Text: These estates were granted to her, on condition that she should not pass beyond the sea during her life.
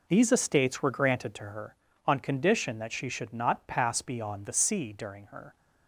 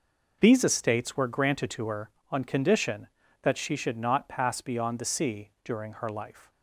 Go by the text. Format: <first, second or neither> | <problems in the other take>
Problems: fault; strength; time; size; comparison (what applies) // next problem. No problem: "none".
second | stops before "life"; at 5.5 s